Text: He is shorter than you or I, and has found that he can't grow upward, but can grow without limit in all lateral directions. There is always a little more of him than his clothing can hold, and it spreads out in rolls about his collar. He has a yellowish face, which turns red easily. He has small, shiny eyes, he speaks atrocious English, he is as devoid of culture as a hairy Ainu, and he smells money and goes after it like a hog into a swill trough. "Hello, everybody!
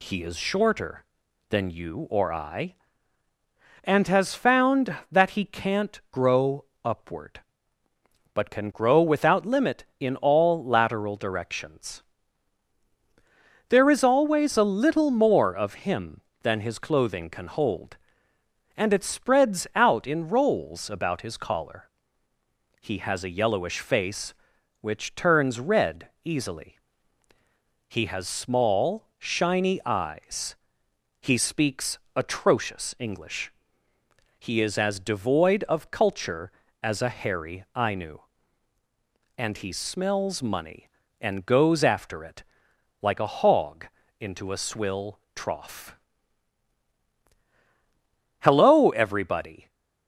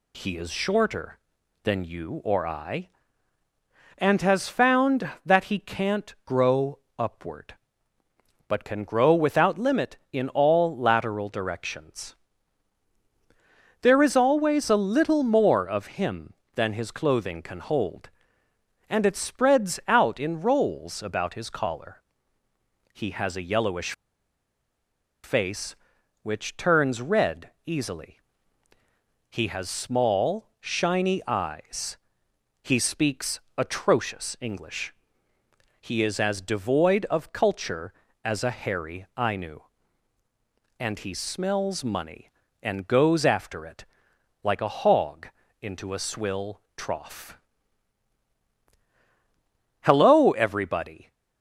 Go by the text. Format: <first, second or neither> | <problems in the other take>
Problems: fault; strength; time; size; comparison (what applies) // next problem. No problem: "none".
first | pauses between "grow" and "upward"; slight; at 6.7 s; 0.20 s long; slight in the first // pauses between "yellowish" and "face"; strong; at 23.9 s; 1.3 s long // pauses between "red" and "easily"; slight; at 27.5 s; 0.16 s long; slight in the first // pauses between "speaks" and "atrocious"; slight; at 33.3 s; 0.16 s long; slight in the first // pauses between "it" and "like"; noticeable; at 43.8 s; 0.58 s long; noticeable in the first // pauses between "hog" and "into"; slight; at 45.2 s; 0.32 s long; slight in the first // pauses between "swill" and "trough"; slight; at 46.6 s; 0.16 s long; slight in the first